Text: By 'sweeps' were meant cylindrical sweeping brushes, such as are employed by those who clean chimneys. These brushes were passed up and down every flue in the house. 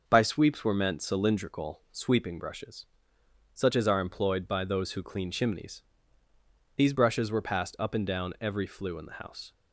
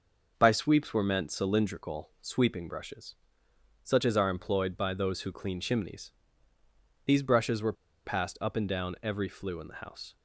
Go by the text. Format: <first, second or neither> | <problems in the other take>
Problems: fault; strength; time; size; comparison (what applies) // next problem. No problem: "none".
first | pauses between "were" and "passed"; slight; at 7.7 s; 0.32 s long